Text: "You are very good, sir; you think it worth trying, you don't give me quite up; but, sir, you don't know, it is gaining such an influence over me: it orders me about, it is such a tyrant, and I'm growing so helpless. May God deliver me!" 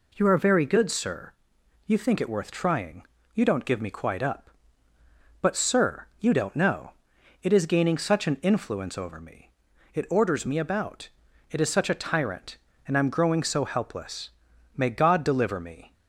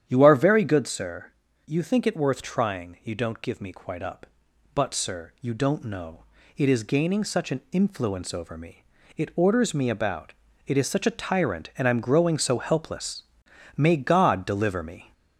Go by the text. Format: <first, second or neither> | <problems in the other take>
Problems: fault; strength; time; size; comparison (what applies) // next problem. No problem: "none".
first | gets louder; slight; throughout; 2 dB // starts louder than the rest; strong; until 1.0 s; 9.5 dB